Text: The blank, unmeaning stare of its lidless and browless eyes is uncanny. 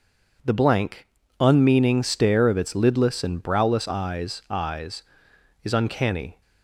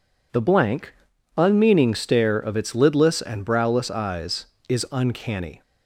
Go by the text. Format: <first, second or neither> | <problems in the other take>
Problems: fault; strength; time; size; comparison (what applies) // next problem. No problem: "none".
second | says "eyes" twice; at 4.4 s